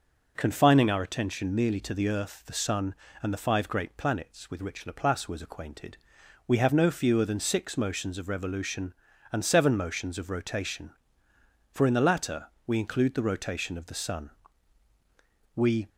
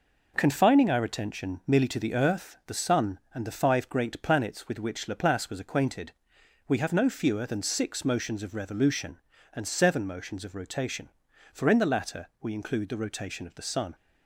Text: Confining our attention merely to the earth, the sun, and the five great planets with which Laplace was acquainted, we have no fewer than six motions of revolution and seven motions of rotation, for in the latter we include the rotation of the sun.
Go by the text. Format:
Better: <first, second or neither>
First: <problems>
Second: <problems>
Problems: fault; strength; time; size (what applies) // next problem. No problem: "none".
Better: second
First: pauses between "latter" and "we"; slight; at 12.4 s; 0.18 s long // goes on to say "We"; slight; from 15.5 s on; 0.34 s long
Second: none